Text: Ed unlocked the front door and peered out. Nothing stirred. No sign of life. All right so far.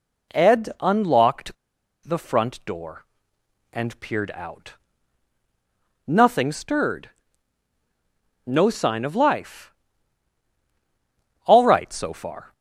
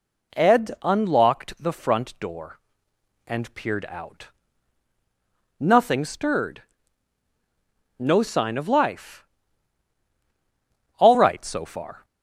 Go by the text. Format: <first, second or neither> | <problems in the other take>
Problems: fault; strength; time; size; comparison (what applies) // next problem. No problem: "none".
second | pauses between "unlocked" and "the"; noticeable; at 1.5 s; 0.50 s long